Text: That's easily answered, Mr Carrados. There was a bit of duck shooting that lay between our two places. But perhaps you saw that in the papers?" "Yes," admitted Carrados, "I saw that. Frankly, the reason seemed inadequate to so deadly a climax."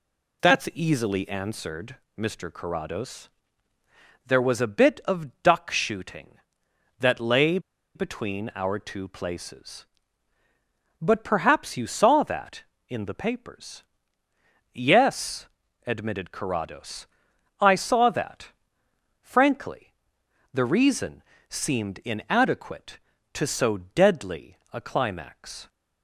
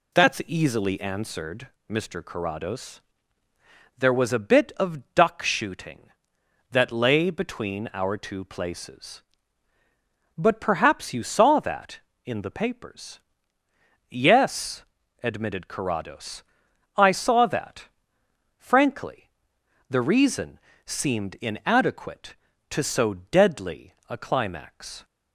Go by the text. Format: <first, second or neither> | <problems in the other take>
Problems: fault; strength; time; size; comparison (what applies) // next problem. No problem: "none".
second | pauses between "lay" and "between"; at 7.5 s; 0.36 s long // pauses between "reason" and "seemed"; slight; at 21.2 s; 0.26 s long; slight in the second